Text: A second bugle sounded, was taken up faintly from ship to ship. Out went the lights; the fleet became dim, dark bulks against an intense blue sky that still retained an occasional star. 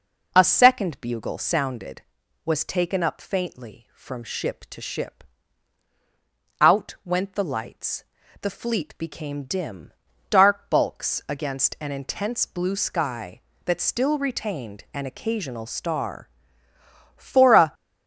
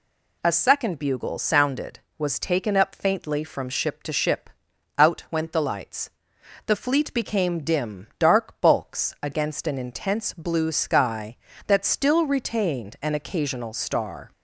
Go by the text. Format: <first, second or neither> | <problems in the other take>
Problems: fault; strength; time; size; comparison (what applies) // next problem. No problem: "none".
second | goes on to say "For a"; from 17.1 s on; 0.56 s long